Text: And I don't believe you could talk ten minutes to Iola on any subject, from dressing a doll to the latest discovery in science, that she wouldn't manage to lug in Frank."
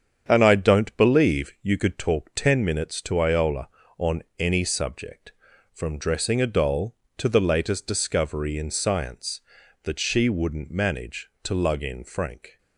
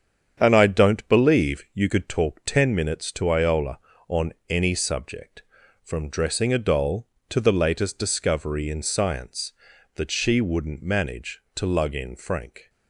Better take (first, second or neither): neither